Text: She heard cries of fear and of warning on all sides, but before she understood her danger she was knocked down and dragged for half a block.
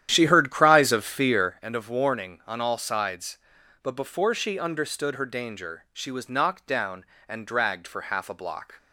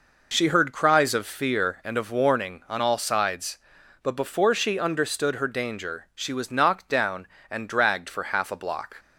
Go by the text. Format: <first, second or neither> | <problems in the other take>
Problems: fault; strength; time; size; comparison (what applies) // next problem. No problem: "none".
second | starts louder than the rest; strong; until 1.6 s; 10.5 dB